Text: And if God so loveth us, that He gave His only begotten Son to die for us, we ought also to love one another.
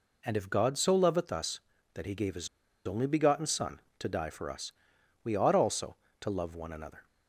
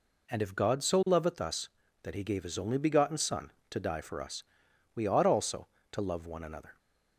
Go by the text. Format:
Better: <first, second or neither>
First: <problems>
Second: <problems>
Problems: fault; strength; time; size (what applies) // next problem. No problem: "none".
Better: second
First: pauses between "His" and "only"; at 2.4 s; 0.38 s long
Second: none